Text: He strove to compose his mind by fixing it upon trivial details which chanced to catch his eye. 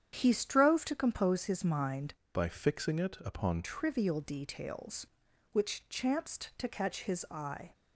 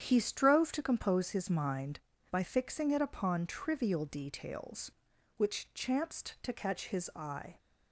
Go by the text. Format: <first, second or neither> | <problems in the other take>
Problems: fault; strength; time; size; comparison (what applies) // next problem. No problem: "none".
second | starts louder than the rest; strong; until 1.1 s; 9 dB; strong in the second // changes voice from "by" to "upon"; from 2.3 to 3.6 s; 1.3 s long